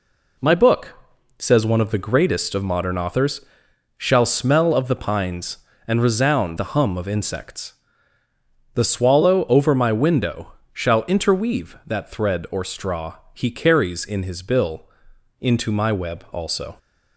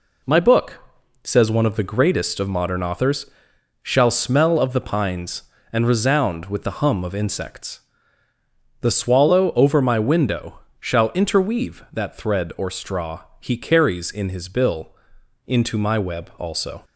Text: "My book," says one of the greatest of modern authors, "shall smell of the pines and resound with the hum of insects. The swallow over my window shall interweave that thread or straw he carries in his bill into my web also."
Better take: second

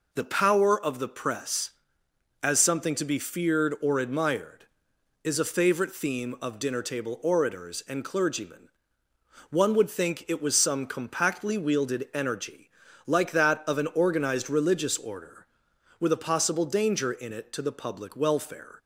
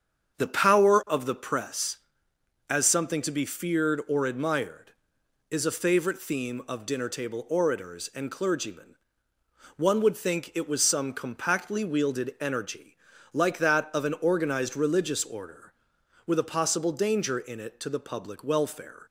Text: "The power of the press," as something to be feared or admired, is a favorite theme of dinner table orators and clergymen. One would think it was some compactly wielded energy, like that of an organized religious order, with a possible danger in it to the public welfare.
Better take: first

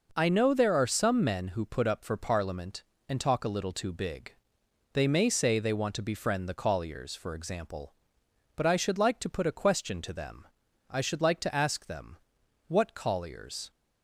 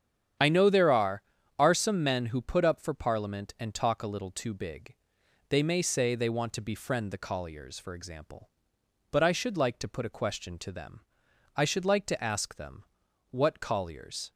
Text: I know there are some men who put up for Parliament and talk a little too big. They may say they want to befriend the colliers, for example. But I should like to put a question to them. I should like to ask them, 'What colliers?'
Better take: first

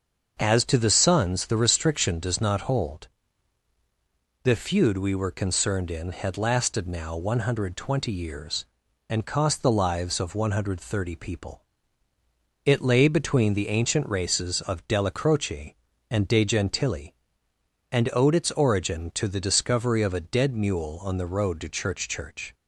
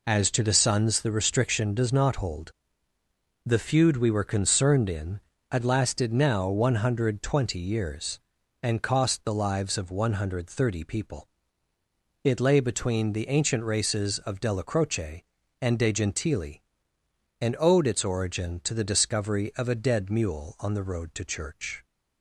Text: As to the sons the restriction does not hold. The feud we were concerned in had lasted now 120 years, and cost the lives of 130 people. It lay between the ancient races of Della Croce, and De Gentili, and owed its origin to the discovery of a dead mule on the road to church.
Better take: second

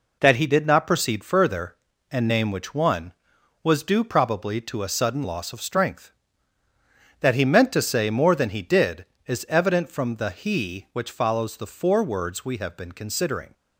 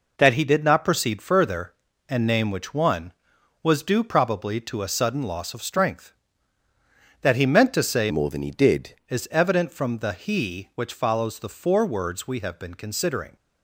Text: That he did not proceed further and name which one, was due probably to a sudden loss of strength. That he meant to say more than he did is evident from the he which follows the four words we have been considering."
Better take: first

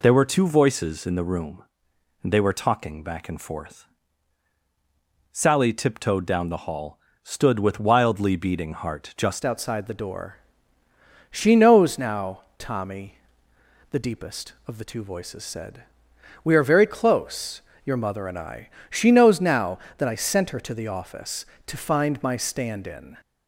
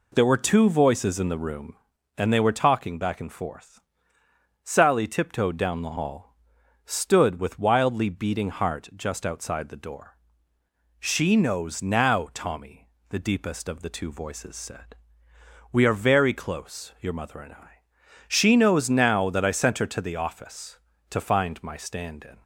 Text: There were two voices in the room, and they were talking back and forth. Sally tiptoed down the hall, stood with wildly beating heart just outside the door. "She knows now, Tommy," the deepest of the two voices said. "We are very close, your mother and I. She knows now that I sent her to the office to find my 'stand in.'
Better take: second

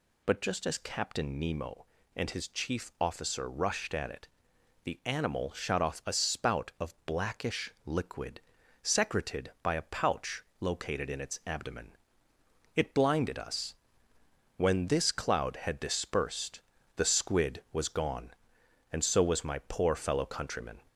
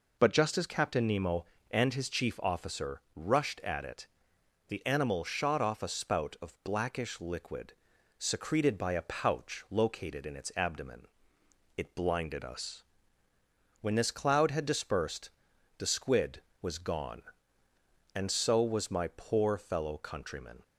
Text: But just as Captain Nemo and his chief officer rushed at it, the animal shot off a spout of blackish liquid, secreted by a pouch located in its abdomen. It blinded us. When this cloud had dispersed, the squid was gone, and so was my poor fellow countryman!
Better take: second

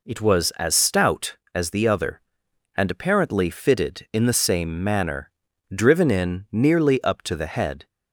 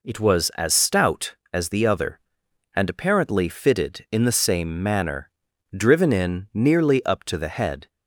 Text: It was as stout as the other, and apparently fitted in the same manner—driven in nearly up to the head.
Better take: neither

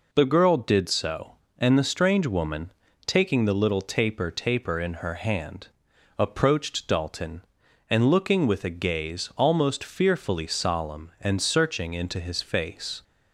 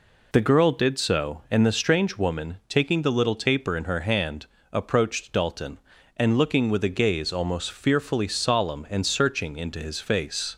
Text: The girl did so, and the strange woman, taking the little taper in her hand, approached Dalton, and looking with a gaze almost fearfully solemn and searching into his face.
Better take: second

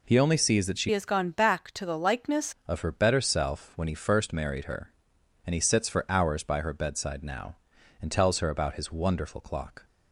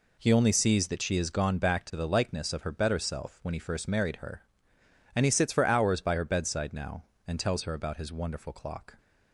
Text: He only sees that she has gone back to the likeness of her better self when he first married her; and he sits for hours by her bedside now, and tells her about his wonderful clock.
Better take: second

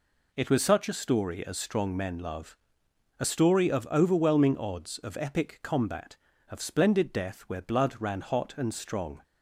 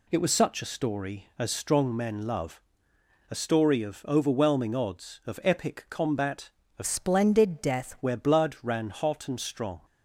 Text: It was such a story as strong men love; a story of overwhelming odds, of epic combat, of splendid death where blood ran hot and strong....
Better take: first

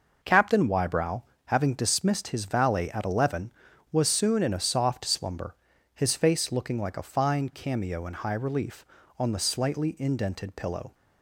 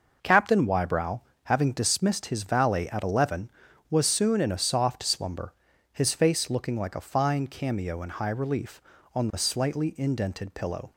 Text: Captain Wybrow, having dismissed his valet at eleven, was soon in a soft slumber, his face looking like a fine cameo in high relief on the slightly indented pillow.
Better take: neither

